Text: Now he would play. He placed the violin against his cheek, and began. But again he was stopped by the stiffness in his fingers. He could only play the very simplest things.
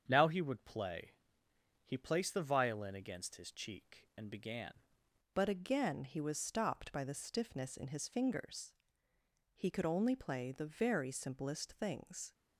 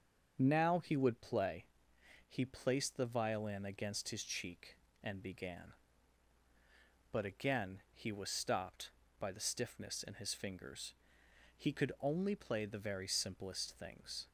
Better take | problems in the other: second | starts louder than the rest; strong; until 1.0 s; 7.5 dB; also in the second // changes voice at "But"; from 5.3 s on; 7.0 s long

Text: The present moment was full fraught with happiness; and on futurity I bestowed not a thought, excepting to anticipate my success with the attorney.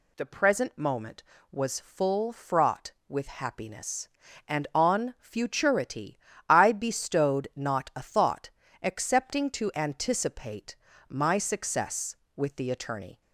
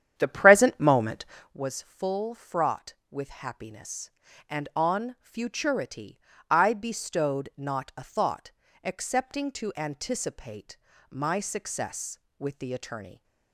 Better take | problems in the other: first | starts louder than the rest; strong; until 1.6 s; 9.5 dB // pauses between "futurity" and "I"; slight; at 6.1 s; 0.30 s long; slight in the first // pauses between "anticipate" and "my"; slight; at 10.7 s; 0.32 s long; slight in the first

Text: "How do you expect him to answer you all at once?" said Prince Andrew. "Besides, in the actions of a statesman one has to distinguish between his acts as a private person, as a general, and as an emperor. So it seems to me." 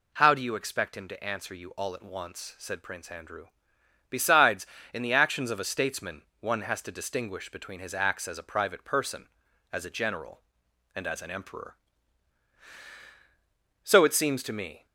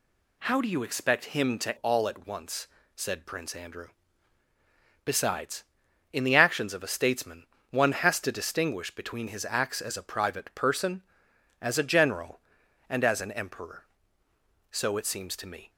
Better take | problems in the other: first | skips "answer you"; at 1.7 s // pauses between "statesman" and "one"; slight; at 7.4 s; 0.24 s long; slight in the first

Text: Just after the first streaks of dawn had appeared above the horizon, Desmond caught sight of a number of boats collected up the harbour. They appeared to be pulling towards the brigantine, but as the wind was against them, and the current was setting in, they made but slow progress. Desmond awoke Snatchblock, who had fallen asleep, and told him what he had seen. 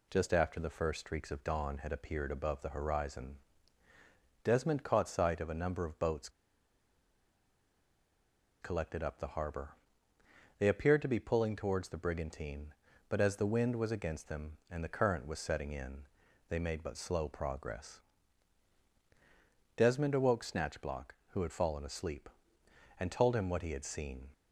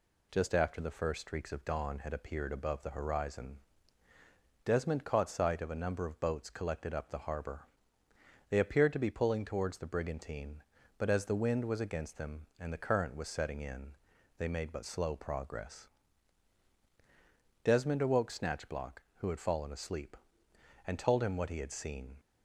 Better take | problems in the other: second | pauses between "boats" and "collected"; strong; at 6.2 s; 2.3 s long

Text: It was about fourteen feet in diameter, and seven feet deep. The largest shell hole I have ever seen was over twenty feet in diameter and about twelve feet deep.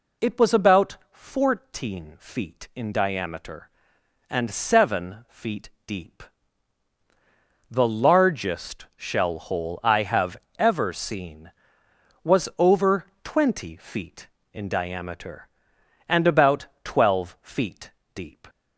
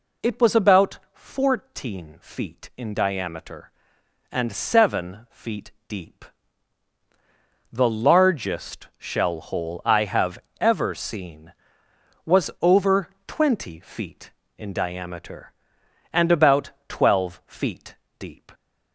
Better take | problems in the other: neither | pauses between "about" and "fourteen"; slight; the same in both // pauses between "feet" and "deep"; slight; the same in both // pauses between "have" and "ever"; slight; the same in both // pauses between "over" and "twenty"; slight; the same in both // pauses between "about" and "twelve"; slight; the same in both // pauses between "feet" and "deep"; slight; the same in both

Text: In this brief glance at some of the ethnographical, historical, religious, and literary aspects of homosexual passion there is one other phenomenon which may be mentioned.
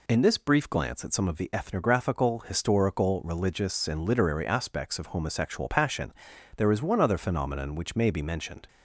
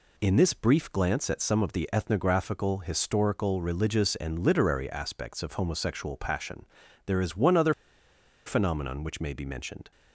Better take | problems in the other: first | pauses between "passion" and "there"; at 6.6 s; 0.40 s long; noticeable in the first // pauses between "other" and "phenomenon"; noticeable; at 7.7 s; 0.73 s long

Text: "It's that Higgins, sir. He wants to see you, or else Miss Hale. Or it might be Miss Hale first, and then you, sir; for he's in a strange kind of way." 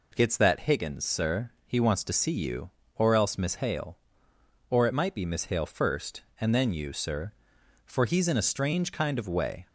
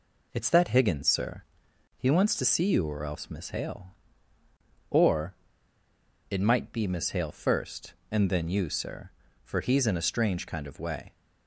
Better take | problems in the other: first | pauses between "Or" and "it"; noticeable; at 5.3 s; 0.96 s long

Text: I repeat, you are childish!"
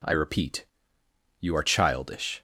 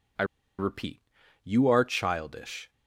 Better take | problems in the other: first | pauses between "I" and "repeat"; slight; at 0.2 s; 0.34 s long

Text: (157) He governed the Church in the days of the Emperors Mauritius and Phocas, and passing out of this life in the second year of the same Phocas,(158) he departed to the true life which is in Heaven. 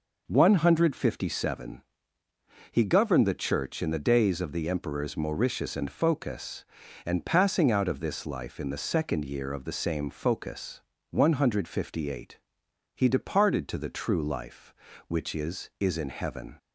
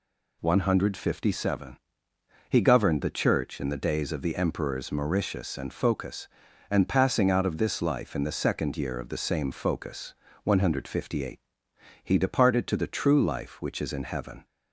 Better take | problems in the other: second | says "is" twice; at 15.7 s

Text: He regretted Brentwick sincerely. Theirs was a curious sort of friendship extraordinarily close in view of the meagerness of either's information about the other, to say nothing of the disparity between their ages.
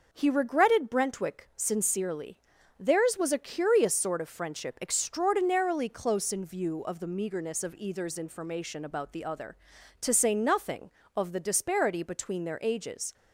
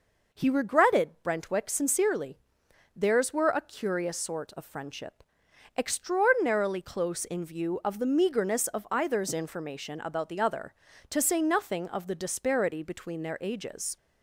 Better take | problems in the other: first | says "were" for "was"; at 3.3 s // pauses between "friendship" and "extraordinarily"; noticeable; at 5.2 s; 0.54 s long

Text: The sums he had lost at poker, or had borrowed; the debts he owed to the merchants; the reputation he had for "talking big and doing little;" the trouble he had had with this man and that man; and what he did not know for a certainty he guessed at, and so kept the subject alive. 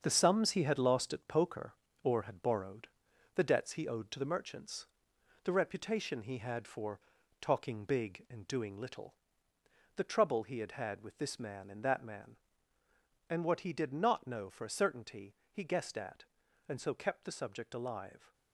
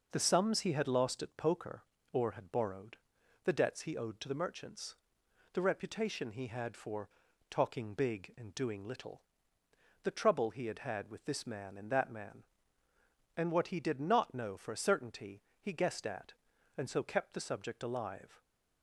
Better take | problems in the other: second | gets quieter; strong; throughout; 7.5 dB // pauses between "for" and "talking"; at 6.9 s; 0.42 s long; also in the second // pauses between "certainty" and "he"; slight; at 15.3 s; 0.16 s long; slight in the second

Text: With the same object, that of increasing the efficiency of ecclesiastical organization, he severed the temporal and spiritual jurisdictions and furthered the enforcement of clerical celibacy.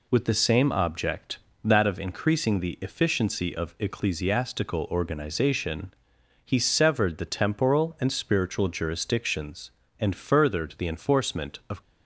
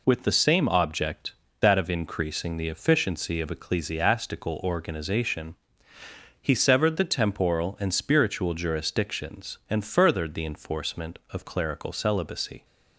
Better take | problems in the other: second | stops before "clerical celibacy"; at 11.8 s

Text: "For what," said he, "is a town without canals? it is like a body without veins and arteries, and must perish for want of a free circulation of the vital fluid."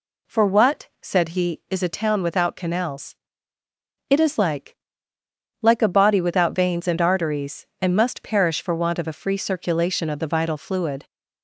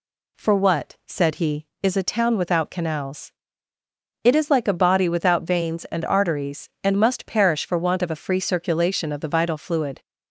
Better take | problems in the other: second | says "like" twice; at 5.6 s

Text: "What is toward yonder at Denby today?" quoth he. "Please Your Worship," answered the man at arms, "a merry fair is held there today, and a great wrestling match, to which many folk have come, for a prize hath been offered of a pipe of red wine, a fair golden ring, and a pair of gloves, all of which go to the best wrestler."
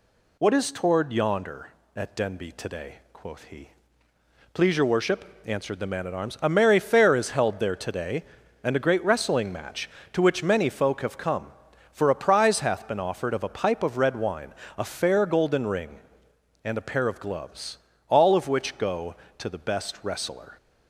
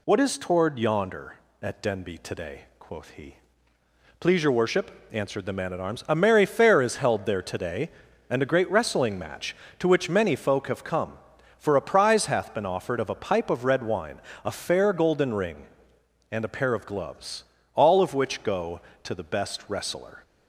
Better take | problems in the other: neither | none

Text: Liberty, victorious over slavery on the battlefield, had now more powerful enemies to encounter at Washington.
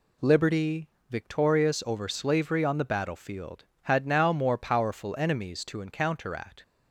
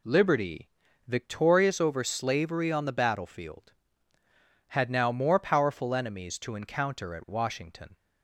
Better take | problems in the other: second | stops before "Washington"; at 6.6 s

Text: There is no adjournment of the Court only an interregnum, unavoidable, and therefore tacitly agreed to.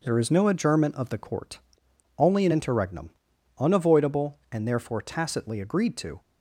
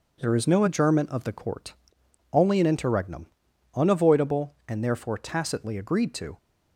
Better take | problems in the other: neither | pauses between "Court" and "only"; noticeable; the same in both

